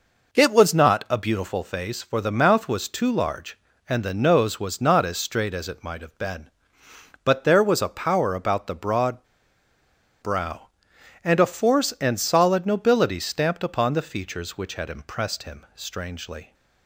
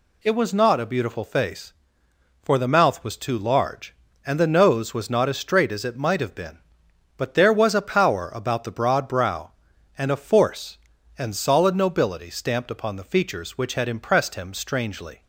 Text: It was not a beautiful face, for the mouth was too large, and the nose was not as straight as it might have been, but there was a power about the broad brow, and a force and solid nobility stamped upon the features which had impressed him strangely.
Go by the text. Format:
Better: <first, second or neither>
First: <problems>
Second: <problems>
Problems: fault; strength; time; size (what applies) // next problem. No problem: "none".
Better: second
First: pauses between "broad" and "brow"; noticeable; at 9.2 s; 0.97 s long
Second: none